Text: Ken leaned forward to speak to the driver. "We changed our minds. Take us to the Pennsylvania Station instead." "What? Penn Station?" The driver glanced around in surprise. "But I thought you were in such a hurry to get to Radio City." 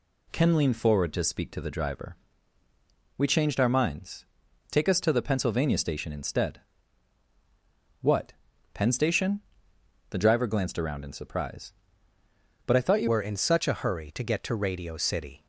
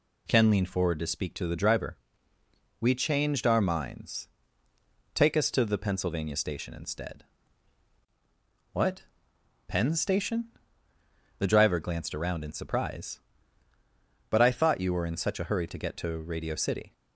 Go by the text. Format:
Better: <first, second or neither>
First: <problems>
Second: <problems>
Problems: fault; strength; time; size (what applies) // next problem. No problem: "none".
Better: second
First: changes voice at "were"; from 13.0 s on; 2.4 s long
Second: none